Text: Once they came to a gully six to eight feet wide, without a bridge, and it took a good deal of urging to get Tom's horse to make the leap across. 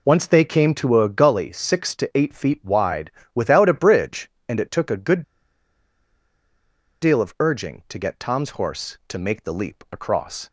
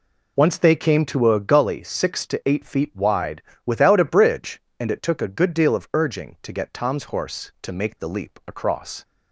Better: second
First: pauses between "good" and "deal"; strong; at 5.2 s; 1.8 s long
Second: none

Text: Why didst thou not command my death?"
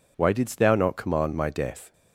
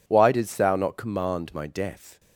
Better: neither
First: none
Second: none

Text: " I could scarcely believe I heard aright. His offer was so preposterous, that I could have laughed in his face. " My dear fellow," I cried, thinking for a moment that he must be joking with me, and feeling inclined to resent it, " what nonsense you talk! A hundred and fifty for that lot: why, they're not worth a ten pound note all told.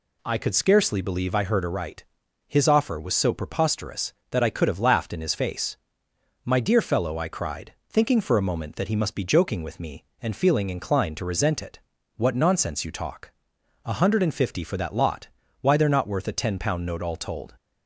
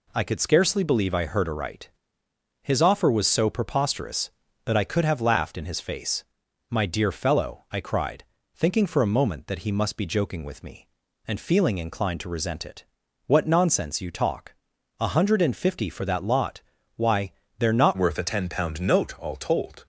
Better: first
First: none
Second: changes voice at "worth"; from 17.9 s on; 1.9 s long

